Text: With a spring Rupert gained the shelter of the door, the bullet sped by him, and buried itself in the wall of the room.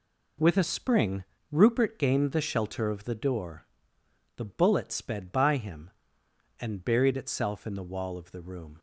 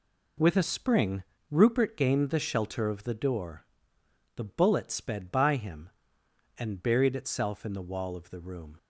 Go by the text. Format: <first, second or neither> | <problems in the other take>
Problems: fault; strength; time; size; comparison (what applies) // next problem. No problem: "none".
neither | pauses between "spring" and "Rupert"; slight; the same in both